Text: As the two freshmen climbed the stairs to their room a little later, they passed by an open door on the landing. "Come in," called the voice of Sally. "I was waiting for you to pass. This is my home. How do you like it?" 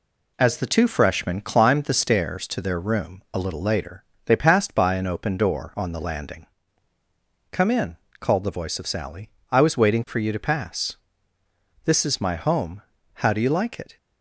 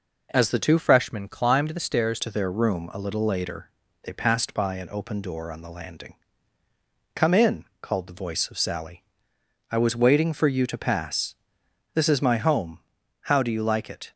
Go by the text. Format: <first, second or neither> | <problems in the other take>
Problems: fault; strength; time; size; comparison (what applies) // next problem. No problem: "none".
first | changes voice from "freshmen" to "stairs"; from 0.7 to 2.1 s; 1.4 s long